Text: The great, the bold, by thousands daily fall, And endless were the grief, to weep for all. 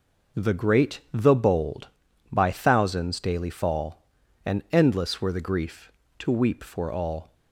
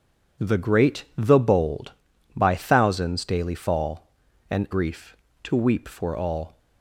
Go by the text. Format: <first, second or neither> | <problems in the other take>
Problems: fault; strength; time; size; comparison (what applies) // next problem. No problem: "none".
first | skips "endless were the"; at 4.6 s